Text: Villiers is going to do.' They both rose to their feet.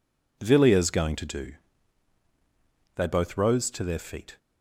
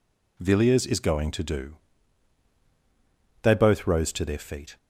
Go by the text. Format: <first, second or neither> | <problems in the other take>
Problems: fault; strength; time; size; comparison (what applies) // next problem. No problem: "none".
second | skips "is"; at 0.9 s